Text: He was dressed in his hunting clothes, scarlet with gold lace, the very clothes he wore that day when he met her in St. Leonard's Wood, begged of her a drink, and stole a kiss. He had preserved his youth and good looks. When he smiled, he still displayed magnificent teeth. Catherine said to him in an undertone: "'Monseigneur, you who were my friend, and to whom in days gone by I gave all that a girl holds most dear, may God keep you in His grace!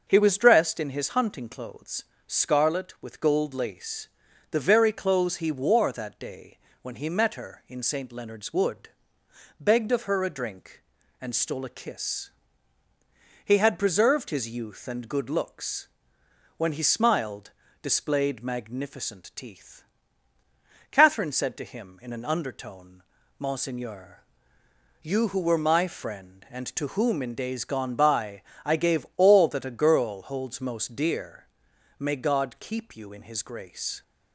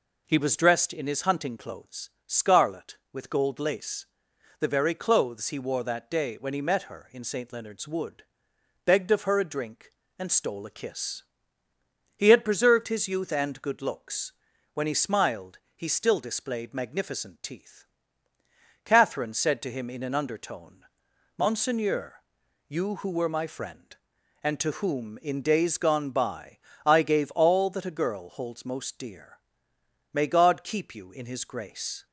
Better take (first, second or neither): second